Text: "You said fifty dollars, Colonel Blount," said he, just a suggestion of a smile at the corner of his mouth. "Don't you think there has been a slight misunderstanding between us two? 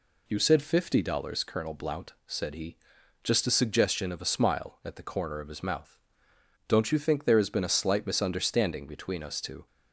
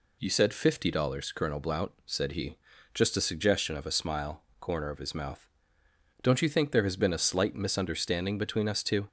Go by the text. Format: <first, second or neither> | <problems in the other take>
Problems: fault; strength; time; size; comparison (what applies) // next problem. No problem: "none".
first | skips "at the"; at 4.5 s